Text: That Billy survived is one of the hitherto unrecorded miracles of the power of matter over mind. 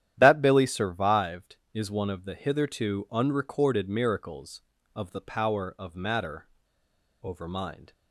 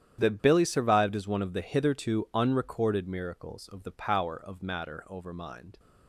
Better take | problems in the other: second | starts louder than the rest; strong; until 1.1 s; 11 dB; strong in the second // pauses between "matter" and "over"; noticeable; at 6.4 s; 0.76 s long

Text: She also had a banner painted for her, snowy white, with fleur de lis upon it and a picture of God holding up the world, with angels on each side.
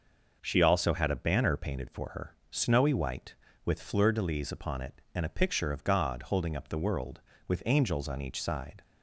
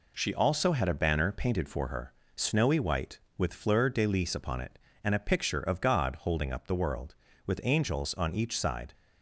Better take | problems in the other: neither | none

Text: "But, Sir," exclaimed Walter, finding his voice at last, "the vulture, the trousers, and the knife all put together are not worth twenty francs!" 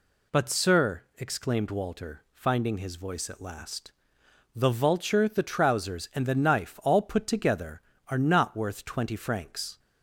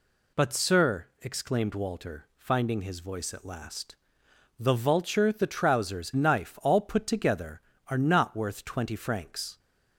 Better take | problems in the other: first | skips "and the"; at 6.1 s

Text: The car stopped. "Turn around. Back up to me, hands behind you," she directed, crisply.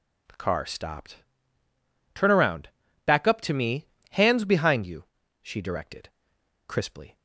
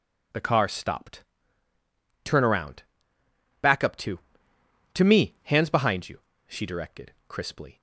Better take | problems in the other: first | says "to" twice; at 4.9 s

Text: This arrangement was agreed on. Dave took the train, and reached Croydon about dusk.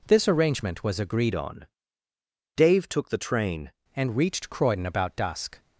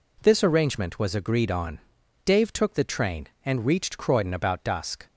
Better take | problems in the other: second | changes voice from "on" to "train"; from 1.3 to 3.7 s; 2.4 s long

